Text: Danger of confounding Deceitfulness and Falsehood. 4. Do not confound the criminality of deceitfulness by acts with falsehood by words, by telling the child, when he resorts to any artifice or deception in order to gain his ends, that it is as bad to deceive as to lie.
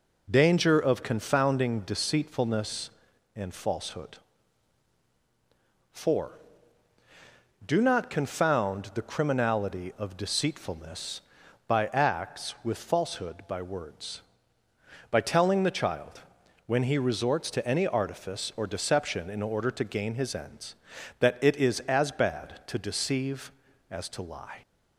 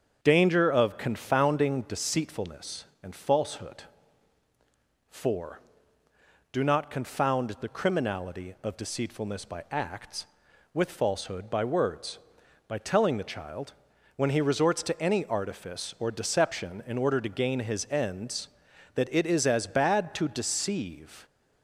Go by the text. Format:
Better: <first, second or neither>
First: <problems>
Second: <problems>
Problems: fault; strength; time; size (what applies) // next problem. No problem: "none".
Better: first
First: none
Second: starts louder than the rest; until 1.2 s; 7 dB // stops before "as to lie"; at 21.2 s